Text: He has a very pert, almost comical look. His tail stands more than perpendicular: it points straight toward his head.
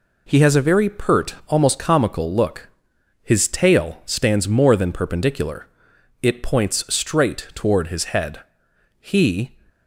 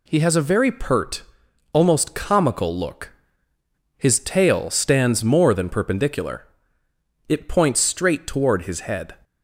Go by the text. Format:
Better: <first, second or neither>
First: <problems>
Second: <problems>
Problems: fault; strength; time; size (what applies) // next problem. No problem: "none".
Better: second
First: goes on to say "He"; from 8.9 s on; 0.54 s long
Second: none